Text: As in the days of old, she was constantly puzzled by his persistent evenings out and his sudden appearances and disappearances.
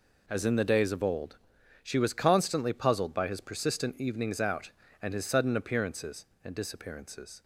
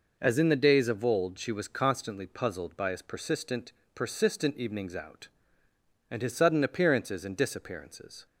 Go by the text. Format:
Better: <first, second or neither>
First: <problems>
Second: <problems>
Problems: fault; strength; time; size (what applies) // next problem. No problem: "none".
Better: first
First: none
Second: says "persistent" twice; at 3.9 s